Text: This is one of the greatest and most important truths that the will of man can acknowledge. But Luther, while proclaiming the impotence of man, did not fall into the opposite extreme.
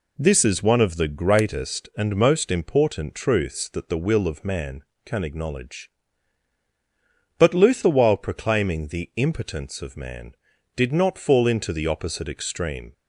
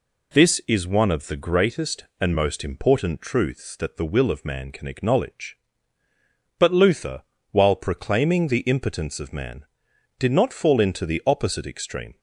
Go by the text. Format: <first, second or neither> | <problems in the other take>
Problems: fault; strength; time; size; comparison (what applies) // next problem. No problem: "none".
neither | none